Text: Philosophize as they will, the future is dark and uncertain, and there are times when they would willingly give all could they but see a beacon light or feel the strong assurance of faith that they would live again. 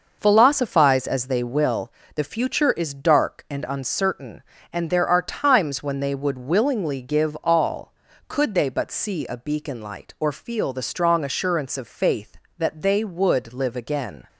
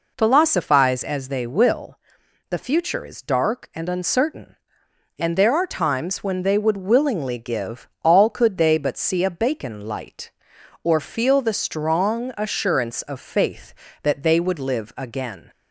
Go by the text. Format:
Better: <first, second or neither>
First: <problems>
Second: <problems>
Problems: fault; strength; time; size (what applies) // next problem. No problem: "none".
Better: first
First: none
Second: pauses between "give" and "all"; slight; at 7.8 s; 0.16 s long // says "bacon" for "beacon"; at 9.2 s